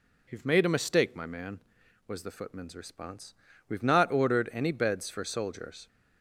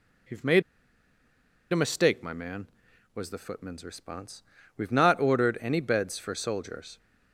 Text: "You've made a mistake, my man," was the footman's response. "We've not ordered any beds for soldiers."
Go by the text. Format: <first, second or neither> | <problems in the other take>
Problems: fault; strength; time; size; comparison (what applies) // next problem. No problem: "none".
first | pauses between "made" and "a"; at 0.6 s; 1.0 s long